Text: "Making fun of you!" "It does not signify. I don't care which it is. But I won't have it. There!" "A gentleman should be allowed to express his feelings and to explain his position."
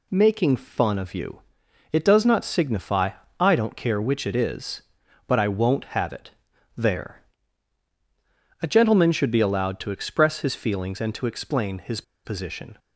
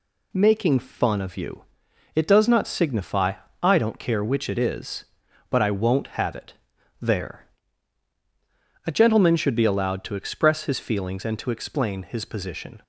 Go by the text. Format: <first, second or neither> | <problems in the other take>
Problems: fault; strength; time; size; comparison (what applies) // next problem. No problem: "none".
second | pauses between "his" and "position"; slight; at 12.0 s; 0.22 s long